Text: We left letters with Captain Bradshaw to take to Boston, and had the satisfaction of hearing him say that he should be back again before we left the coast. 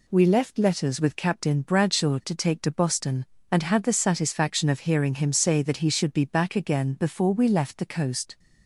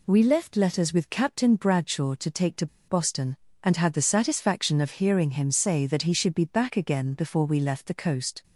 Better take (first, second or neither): first